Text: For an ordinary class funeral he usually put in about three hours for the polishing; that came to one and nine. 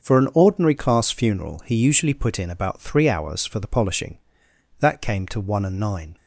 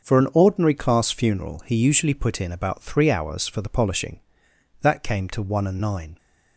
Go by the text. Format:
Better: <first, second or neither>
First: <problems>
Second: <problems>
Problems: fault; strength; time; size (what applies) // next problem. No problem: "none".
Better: neither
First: starts louder than the rest; until 1.1 s; 6.5 dB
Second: starts louder than the rest; until 1.1 s; 6.5 dB